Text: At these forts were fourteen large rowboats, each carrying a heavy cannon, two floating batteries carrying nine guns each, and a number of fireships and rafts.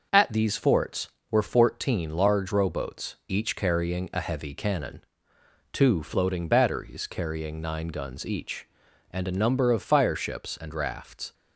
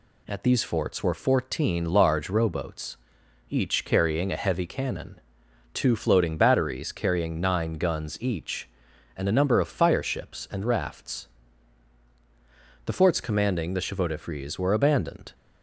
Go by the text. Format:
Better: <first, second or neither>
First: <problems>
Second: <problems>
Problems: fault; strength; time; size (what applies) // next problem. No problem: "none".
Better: first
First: none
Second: goes on to say "The forts commanding the chevaux de frise were abandoned"; strong; from 12.8 s on; 2.4 s long